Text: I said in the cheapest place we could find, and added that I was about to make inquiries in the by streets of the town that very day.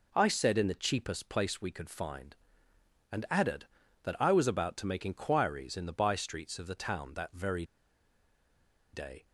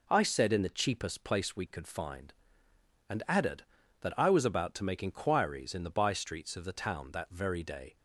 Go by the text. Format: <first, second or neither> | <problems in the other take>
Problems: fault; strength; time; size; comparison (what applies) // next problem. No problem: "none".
second | pauses between "very" and "day"; strong; at 7.6 s; 1.2 s long